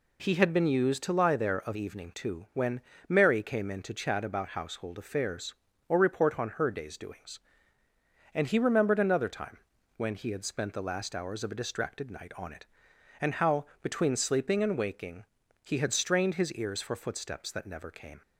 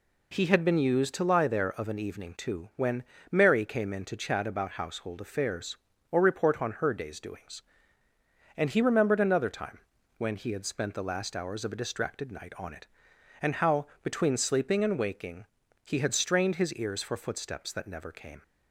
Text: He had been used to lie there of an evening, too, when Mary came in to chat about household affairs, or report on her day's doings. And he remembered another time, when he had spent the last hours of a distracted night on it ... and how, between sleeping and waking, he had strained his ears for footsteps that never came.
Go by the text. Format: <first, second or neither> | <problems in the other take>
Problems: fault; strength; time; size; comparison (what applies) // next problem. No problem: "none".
second | skips "an"; at 1.7 s // pauses between "when" and "Mary"; slight; at 2.8 s; 0.26 s long; slight in the second